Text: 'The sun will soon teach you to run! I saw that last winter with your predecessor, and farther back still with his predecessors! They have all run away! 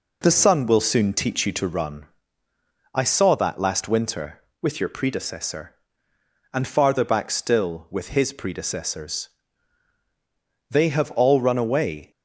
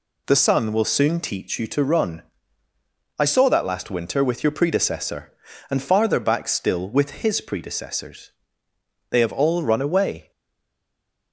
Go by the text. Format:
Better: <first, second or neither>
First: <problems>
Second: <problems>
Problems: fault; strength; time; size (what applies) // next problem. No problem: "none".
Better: first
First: none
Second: stays silent after the last word; from 10.3 s on; 1.0 s long